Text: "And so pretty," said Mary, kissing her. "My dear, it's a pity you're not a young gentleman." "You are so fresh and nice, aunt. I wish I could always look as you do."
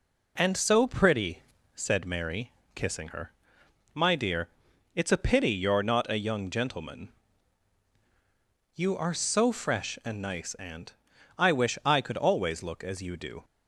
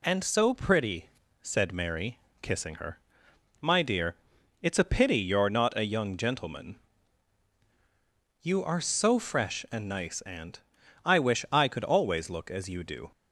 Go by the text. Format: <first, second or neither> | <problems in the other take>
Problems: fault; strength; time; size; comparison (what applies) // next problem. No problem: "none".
second | starts louder than the rest; slight; until 1.9 s; 3 dB